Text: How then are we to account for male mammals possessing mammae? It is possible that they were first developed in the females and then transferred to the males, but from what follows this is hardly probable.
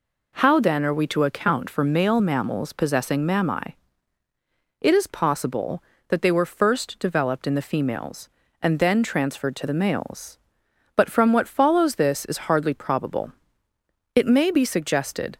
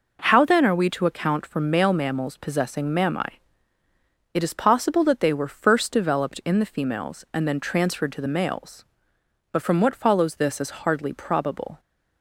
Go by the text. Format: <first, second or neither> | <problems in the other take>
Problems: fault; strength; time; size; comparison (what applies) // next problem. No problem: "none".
second | goes on to say "It may be suggested"; noticeable; from 14.1 s on; 1.2 s long